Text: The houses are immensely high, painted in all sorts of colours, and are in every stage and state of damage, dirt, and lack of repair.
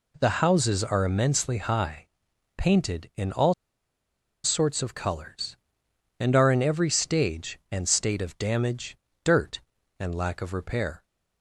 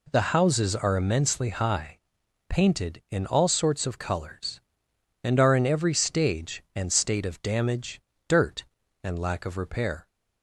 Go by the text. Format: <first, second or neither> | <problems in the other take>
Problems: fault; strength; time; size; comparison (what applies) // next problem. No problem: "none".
second | pauses between "all" and "sorts"; noticeable; at 3.5 s; 0.90 s long